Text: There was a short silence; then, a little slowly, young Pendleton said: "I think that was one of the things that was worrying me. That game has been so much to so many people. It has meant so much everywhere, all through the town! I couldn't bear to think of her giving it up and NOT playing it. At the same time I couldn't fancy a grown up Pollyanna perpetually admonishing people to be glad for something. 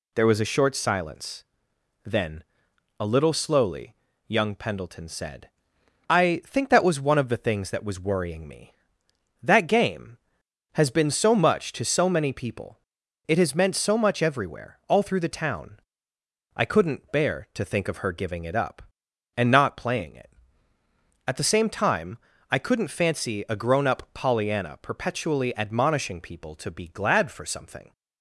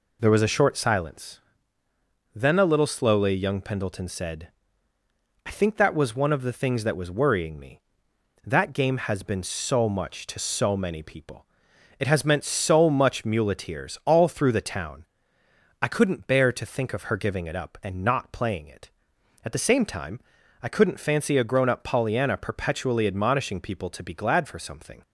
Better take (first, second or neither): first